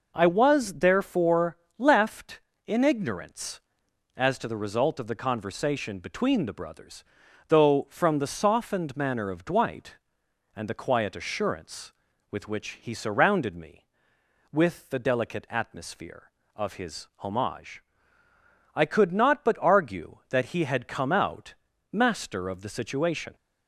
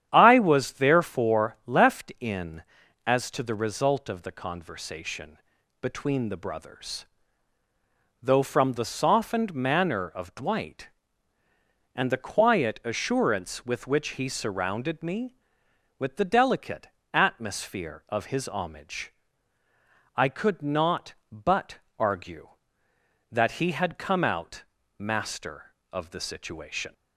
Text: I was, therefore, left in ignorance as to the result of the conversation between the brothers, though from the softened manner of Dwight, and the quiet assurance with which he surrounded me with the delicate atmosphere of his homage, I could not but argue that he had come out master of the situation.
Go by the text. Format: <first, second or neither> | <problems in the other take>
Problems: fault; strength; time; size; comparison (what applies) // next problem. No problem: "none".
first | starts louder than the rest; strong; until 1.1 s; 10 dB // skips "ignorance"; at 2.8 s // pauses between "conversation" and "between"; noticeable; at 5.3 s; 0.46 s long // pauses between "delicate" and "atmosphere"; slight; at 16.8 s; 0.24 s long // pauses between "but" and "argue"; slight; at 21.7 s; 0.20 s long // pauses between "out" and "master"; slight; at 24.6 s; 0.34 s long; slight in the first